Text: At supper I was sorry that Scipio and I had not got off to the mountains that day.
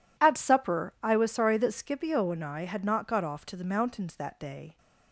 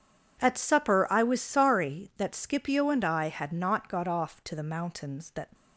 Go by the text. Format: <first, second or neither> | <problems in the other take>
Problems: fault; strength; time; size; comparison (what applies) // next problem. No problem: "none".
first | stops before "day"; at 5.5 s